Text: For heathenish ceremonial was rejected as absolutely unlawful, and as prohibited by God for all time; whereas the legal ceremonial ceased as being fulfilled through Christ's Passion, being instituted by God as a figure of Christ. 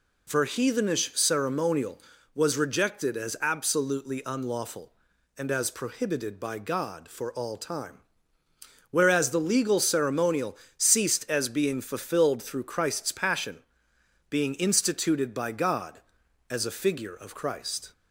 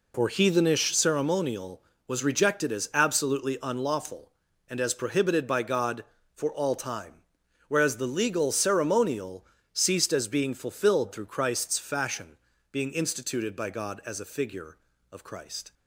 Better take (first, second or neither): first